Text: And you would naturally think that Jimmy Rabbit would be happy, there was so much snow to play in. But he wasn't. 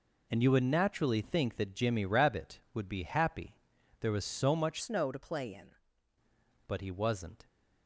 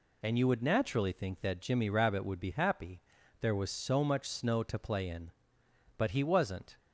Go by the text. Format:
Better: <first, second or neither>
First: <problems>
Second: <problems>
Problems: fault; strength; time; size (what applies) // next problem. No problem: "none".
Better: second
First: changes voice from "snow" to "in"; from 4.7 to 5.7 s; 1.0 s long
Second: none